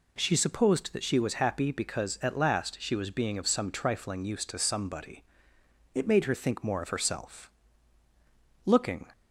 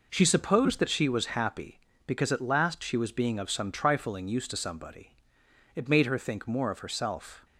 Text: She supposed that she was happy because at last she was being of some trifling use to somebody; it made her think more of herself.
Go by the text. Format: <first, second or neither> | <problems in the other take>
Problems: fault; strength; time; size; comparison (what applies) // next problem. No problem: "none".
second | goes on to say "Looking"; slight; from 8.6 s on; 0.40 s long